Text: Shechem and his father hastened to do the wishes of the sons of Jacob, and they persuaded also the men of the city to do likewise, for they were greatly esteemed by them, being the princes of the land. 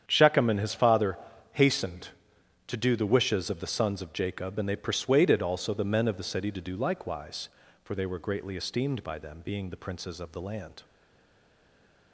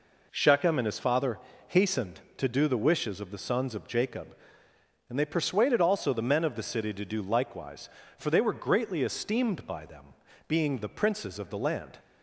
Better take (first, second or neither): second